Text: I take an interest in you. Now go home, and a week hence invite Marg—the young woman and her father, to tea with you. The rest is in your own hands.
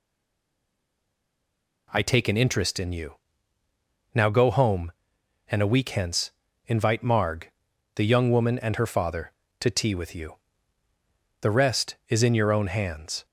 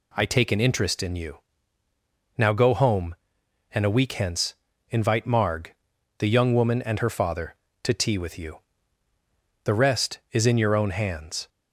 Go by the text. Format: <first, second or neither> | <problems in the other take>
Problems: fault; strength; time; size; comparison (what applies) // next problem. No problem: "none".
second | stays silent before the first word; noticeable; until 1.8 s; 1.8 s long // pauses between "hence" and "invite"; slight; at 6.3 s; 0.36 s long; slight in the second